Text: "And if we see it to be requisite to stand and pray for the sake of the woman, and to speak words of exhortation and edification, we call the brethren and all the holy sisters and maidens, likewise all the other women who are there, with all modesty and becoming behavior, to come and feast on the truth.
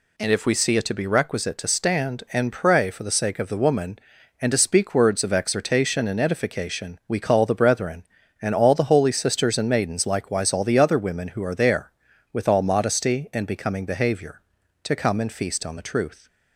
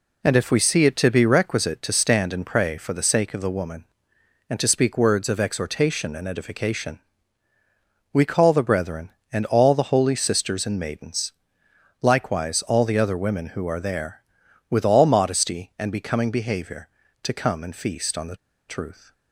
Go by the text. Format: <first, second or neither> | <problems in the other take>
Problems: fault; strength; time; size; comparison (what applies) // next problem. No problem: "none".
first | pauses between "the" and "truth"; slight; at 18.3 s; 0.33 s long